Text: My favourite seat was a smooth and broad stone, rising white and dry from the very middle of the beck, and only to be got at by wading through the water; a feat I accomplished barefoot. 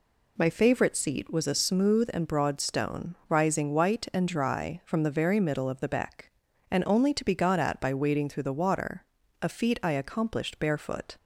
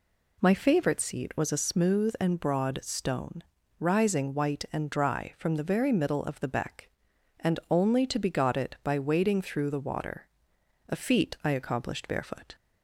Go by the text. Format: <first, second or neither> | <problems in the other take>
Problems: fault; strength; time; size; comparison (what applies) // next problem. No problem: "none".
first | says "it" for "at"; at 8.5 s